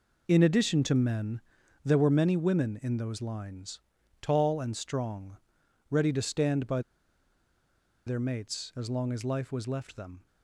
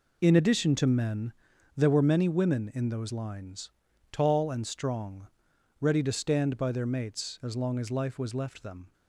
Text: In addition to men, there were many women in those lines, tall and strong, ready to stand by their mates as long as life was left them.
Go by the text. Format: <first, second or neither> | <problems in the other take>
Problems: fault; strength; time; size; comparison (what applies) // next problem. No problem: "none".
second | pauses between "by" and "their"; strong; at 6.7 s; 1.2 s long